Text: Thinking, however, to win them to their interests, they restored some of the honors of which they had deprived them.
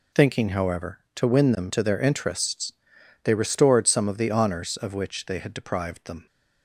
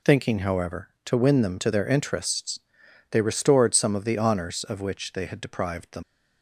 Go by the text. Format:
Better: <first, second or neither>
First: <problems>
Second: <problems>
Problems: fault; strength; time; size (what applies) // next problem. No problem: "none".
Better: first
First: none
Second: leaves "them" unfinished; at 6.0 s; 100 ms